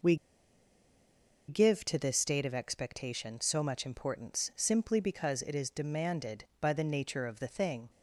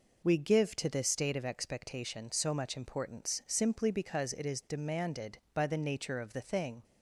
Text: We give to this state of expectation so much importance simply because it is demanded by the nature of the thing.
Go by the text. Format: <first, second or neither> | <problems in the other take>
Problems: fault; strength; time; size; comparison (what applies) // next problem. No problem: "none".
second | pauses between "We" and "give"; strong; at 0.1 s; 1.3 s long